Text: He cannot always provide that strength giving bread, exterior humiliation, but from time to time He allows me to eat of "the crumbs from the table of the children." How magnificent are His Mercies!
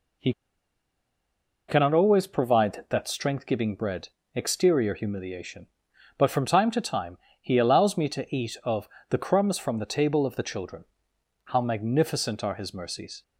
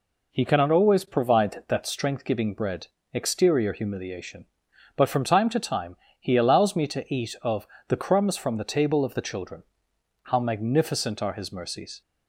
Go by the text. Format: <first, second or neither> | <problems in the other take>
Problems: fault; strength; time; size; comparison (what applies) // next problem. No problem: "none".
second | pauses between "He" and "cannot"; strong; at 0.3 s; 1.3 s long // pauses between "time" and "He"; slight; at 7.1 s; 0.24 s long; slight in the second // pauses between "of" and "the"; slight; at 8.8 s; 0.22 s long; slight in the second